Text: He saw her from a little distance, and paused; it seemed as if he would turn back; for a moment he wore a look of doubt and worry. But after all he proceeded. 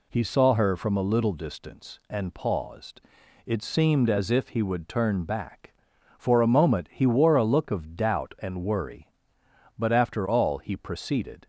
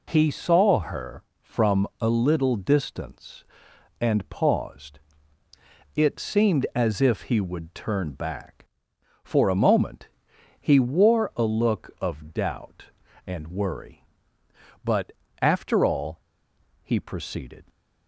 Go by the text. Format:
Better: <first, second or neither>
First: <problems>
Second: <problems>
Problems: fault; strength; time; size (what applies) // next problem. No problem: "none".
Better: first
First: none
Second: pauses between "moment" and "he"; noticeable; at 10.0 s; 0.50 s long // pauses between "But" and "after"; slight; at 15.1 s; 0.30 s long // pauses between "all" and "he"; noticeable; at 16.2 s; 0.61 s long